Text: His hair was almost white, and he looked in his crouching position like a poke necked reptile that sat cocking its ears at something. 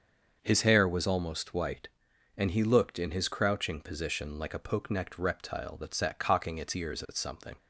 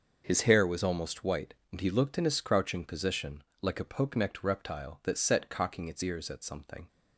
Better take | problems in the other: first | starts louder than the rest; noticeable; until 1.2 s; 6 dB; also in the first // pauses between "position" and "like"; slight; at 3.4 s; 0.18 s long // says "set" for "sat"; at 5.1 s

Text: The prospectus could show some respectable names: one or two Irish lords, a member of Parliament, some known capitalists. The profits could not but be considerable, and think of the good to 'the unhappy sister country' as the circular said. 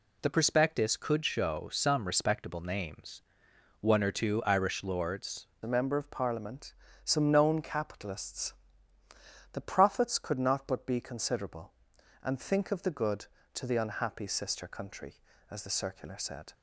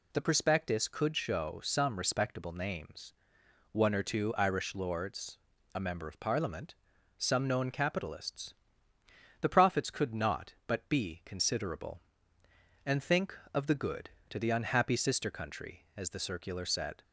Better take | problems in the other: second | changes voice at "a"; from 5.6 s on; 10.9 s long

